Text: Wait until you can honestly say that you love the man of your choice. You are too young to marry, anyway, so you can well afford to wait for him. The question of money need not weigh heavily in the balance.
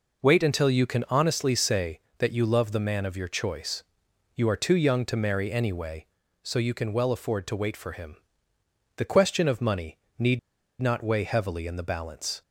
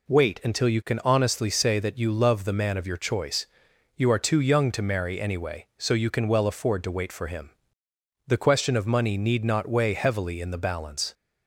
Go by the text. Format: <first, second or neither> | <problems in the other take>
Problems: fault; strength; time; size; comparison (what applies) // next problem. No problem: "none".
second | pauses between "money" and "need"; slight; at 9.9 s; 0.20 s long // pauses between "need" and "not"; at 10.3 s; 0.42 s long